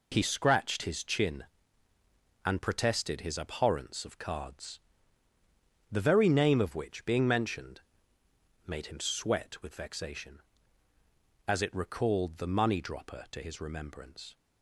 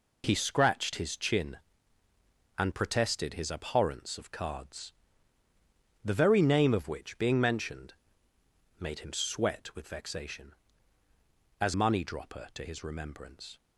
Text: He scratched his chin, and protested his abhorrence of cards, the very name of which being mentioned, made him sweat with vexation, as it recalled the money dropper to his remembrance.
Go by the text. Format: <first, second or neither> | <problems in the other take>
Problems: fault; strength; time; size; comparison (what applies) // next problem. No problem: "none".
first | skips "it recalled the"; at 11.7 s